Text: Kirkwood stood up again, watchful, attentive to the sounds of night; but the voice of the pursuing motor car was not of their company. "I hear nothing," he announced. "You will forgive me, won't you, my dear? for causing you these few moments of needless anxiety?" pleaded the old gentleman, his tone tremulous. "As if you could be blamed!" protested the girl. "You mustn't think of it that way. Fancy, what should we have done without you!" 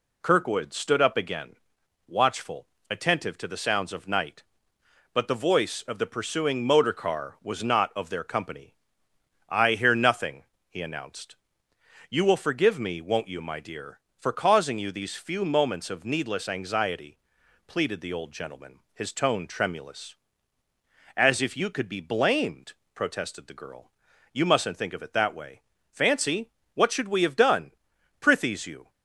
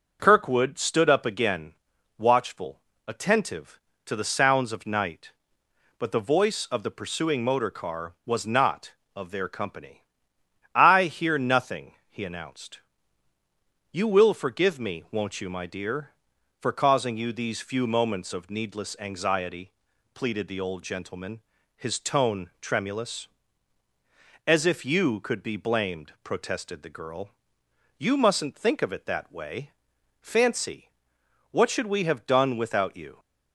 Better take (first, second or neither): second